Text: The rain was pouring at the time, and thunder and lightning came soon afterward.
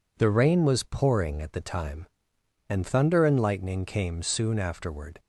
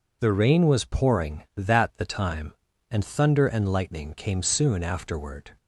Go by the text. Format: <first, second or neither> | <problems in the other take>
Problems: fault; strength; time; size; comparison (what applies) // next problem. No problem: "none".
first | says "that" for "at"; at 1.5 s